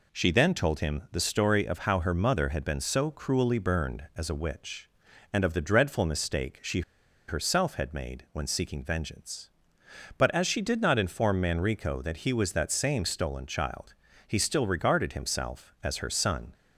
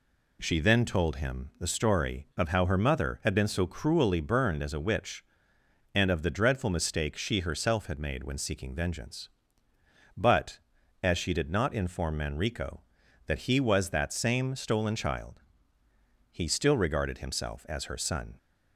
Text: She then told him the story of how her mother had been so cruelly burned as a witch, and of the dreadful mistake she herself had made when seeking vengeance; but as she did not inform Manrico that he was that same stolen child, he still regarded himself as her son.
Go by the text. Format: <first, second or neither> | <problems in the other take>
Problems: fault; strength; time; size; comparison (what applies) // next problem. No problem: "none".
second | pauses between "she" and "herself"; noticeable; at 6.8 s; 0.46 s long